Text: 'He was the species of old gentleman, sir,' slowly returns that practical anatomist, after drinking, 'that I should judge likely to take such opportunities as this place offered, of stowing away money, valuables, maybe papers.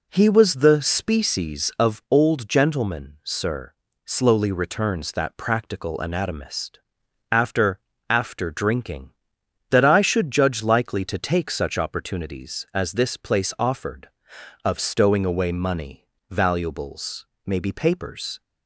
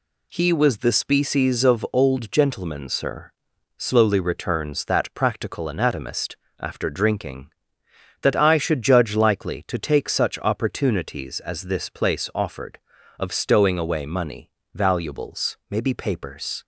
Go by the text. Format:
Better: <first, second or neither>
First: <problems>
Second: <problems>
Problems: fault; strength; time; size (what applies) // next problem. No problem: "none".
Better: second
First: says "after" twice; at 8.0 s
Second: none